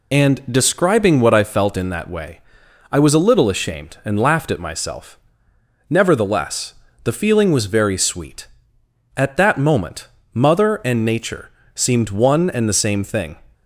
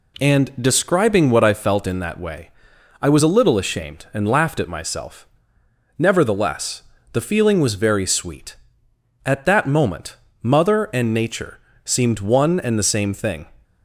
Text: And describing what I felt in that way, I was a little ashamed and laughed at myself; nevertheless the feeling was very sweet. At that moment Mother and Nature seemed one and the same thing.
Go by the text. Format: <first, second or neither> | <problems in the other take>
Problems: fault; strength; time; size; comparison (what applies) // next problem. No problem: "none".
second | loses the start of "And"; at 0.1 s; 50 ms // pauses between "nevertheless" and "the"; slight; at 6.7 s; 0.32 s long; slight in the second // pauses between "moment" and "Mother"; slight; at 10.0 s; 0.24 s long; slight in the second // pauses between "Nature" and "seemed"; slight; at 11.4 s; 0.24 s long; slight in the second